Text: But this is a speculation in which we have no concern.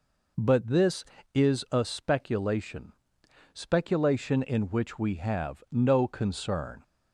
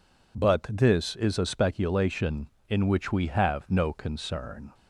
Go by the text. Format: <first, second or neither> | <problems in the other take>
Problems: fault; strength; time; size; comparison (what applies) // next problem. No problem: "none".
second | says "speculation" twice; at 3.5 s